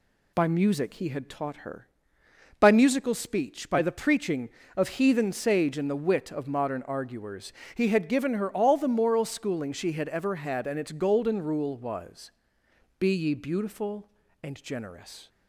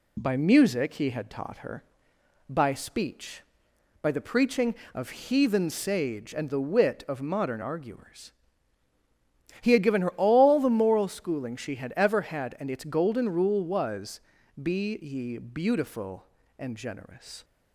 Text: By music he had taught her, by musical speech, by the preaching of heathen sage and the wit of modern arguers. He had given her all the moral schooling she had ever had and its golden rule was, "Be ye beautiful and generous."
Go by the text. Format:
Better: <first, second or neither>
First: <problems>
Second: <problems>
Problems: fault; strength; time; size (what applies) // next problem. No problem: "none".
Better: first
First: none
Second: skips "musical"; at 2.7 s